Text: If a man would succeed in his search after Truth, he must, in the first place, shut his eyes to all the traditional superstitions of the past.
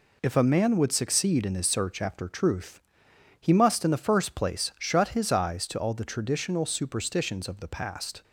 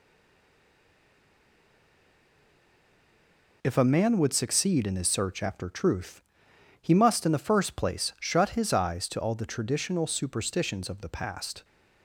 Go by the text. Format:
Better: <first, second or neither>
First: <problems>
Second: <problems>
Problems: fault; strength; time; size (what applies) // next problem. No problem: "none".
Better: first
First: none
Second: stays silent before the first word; strong; until 3.6 s; 3.6 s long